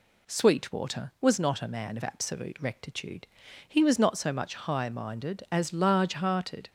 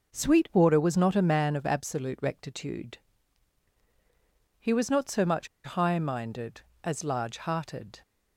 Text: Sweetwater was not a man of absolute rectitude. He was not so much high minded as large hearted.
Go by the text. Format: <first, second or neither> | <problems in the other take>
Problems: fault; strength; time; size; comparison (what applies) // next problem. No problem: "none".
first | pauses between "much" and "high"; slight; at 5.4 s; 0.17 s long